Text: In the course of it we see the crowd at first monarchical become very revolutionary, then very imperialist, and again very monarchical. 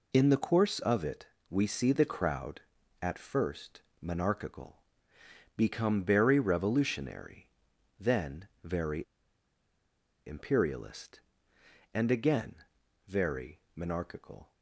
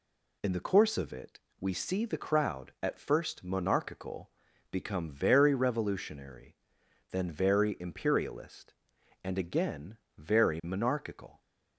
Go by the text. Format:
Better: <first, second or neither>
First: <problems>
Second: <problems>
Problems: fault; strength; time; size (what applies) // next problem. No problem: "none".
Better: second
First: pauses between "it" and "we"; slight; at 1.2 s; 0.22 s long // pauses between "first" and "monarchical"; slight; at 3.7 s; 0.22 s long // pauses between "monarchical" and "become"; noticeable; at 4.8 s; 0.74 s long // pauses between "then" and "very"; slight; at 8.4 s; 0.16 s long // pauses between "very" and "imperialist"; at 9.0 s; 1.2 s long // pauses between "again" and "very"; noticeable; at 12.5 s; 0.54 s long // pauses between "very" and "monarchical"; slight; at 13.5 s; 0.16 s long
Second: pauses between "it" and "we"; slight; at 1.3 s; 0.22 s long // pauses between "monarchical" and "become"; at 4.2 s; 0.42 s long // pauses between "again" and "very"; slight; at 9.9 s; 0.18 s long